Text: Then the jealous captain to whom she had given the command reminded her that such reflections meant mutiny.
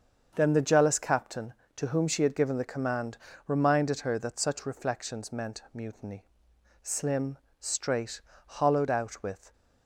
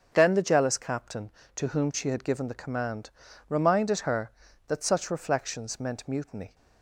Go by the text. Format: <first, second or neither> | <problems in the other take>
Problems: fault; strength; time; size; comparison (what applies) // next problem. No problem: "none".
second | starts louder than the rest; until 1.3 s; 7 dB; also in the second // pauses between "command" and "reminded"; slight; at 3.1 s; 0.30 s long; also in the second // goes on to say "Slim straight hollowed out with"; strong; from 6.8 s on; 2.7 s long